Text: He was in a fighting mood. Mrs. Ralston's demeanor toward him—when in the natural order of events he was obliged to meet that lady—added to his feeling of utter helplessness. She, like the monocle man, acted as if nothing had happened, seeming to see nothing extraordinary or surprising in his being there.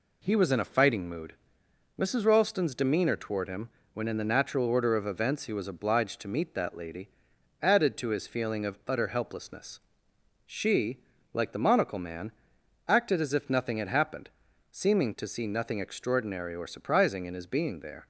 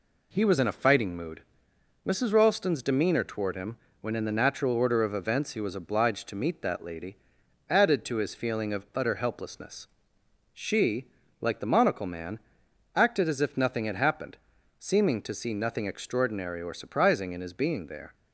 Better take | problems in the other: neither | none

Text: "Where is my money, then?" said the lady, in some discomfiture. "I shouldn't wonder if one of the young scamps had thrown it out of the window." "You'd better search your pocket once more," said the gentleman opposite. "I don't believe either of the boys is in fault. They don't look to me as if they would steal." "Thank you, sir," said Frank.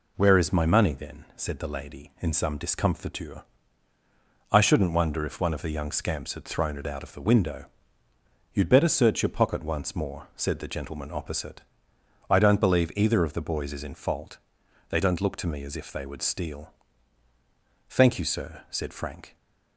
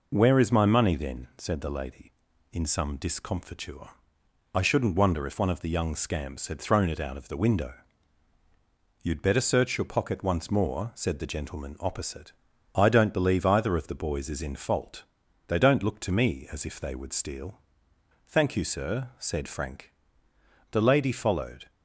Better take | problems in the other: first | goes on to say "The lady followed"; noticeable; from 20.6 s on; 1.0 s long

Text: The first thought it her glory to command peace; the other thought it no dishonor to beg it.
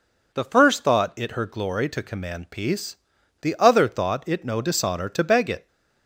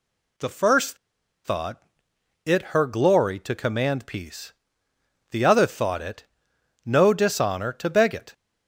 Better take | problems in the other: first | pauses between "first" and "thought"; noticeable; at 0.9 s; 0.47 s long // pauses between "thought" and "it"; noticeable; at 1.8 s; 0.62 s long // pauses between "it" and "no"; noticeable; at 6.2 s; 0.64 s long

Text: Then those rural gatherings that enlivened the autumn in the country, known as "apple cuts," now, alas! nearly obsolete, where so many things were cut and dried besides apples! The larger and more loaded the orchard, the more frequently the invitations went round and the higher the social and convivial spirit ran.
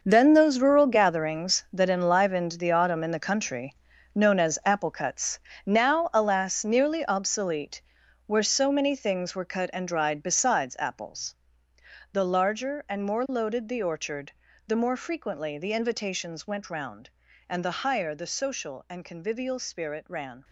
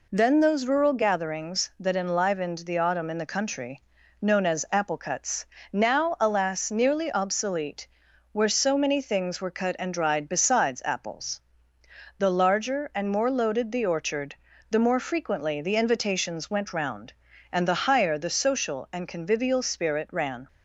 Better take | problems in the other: second | gets quieter; strong; throughout; 11.5 dB

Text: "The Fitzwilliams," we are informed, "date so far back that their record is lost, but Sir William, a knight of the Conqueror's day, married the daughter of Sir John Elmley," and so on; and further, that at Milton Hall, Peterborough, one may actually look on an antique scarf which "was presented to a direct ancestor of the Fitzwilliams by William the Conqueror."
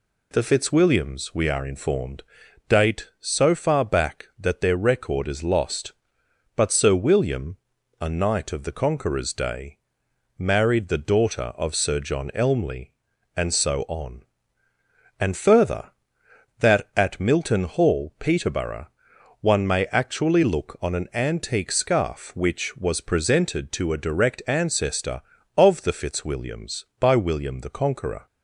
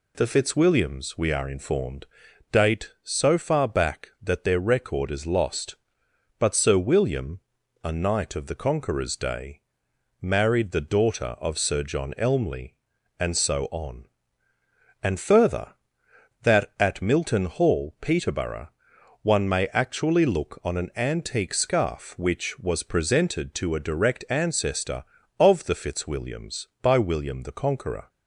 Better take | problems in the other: neither | none

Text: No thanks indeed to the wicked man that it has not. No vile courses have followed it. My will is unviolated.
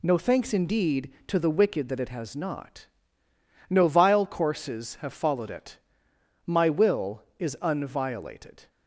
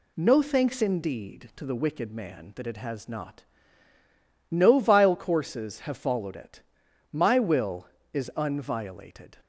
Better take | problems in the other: second | skips "man"; at 1.8 s

